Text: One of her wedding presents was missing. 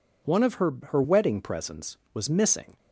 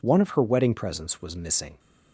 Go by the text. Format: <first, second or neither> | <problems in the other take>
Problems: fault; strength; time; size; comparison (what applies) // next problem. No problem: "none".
second | says "her" twice; at 0.8 s